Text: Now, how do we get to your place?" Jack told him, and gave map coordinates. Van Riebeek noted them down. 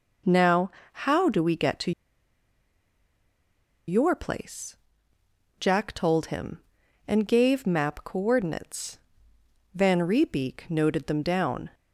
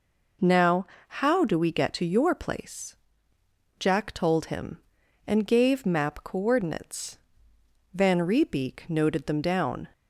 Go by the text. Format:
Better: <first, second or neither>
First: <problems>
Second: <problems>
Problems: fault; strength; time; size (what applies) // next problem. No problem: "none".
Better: second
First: pauses between "to" and "your"; strong; at 1.9 s; 1.9 s long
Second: none